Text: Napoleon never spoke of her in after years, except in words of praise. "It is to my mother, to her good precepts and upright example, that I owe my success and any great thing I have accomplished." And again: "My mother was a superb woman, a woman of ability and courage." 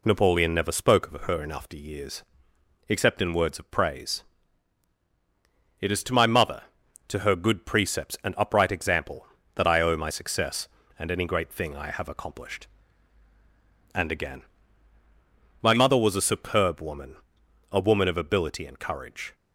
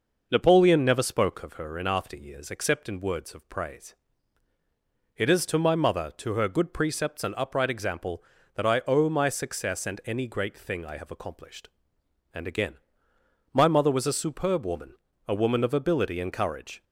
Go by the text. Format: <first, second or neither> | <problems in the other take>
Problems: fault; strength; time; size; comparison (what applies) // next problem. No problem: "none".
first | starts louder than the rest; noticeable; until 1.7 s; 5.5 dB